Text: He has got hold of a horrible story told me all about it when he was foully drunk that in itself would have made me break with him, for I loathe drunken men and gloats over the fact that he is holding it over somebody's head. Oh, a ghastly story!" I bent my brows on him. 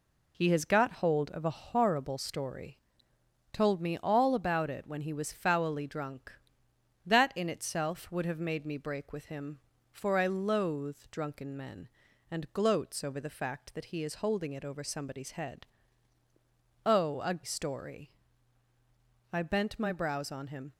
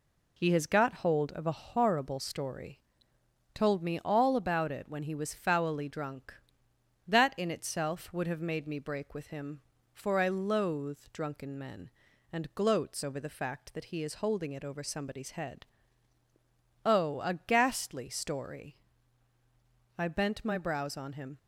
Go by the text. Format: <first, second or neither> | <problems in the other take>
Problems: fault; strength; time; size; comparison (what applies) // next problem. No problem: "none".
second | pauses between "story" and "told"; noticeable; at 2.7 s; 0.76 s long; noticeable in the second // skips "ghastly"; at 17.3 s